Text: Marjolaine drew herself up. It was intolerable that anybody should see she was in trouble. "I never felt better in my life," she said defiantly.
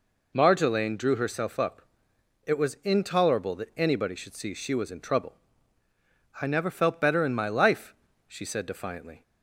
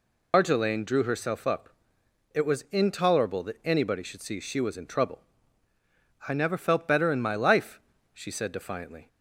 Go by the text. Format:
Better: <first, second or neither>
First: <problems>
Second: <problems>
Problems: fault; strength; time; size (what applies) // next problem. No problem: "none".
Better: first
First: none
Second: loses the start of "Marjolaine"; at 0.3 s; 115 ms